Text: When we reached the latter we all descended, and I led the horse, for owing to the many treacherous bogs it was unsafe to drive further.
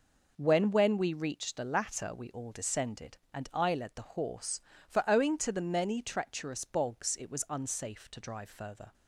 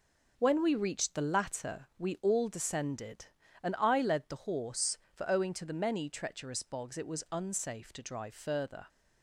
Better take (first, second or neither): second